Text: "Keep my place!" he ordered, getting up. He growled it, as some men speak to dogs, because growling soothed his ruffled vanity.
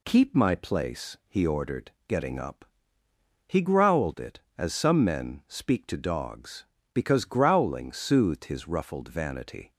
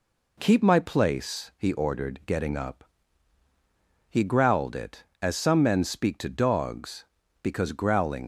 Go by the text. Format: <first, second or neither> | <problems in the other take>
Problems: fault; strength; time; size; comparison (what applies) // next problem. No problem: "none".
first | stops before "soothed his ruffled vanity"; at 8.2 s